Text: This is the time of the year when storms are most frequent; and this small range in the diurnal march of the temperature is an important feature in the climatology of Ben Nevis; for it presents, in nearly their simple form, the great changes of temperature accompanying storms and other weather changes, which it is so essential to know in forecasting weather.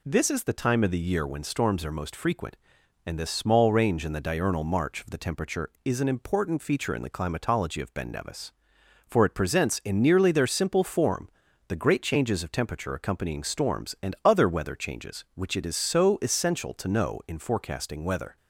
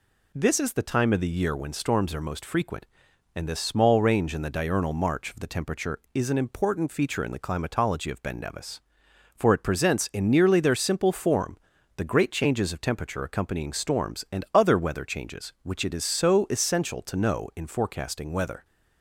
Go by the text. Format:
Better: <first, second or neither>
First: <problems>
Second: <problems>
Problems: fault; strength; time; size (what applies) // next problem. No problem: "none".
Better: neither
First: none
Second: none